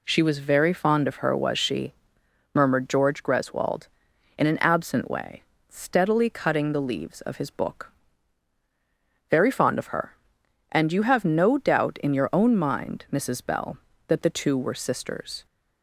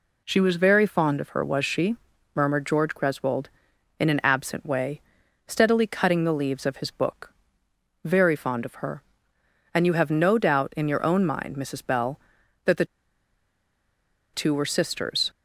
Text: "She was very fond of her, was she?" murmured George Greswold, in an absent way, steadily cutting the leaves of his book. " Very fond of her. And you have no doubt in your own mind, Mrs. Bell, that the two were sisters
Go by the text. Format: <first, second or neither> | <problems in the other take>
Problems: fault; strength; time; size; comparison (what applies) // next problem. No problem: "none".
first | pauses between "the" and "two"; strong; at 12.8 s; 1.4 s long